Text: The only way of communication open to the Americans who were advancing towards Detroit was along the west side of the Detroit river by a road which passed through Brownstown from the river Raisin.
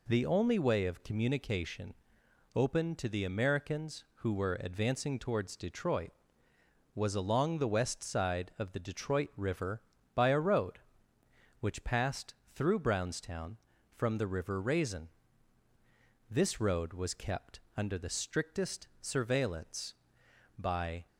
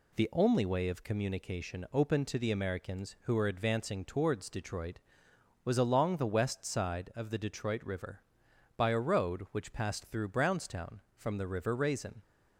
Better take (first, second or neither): second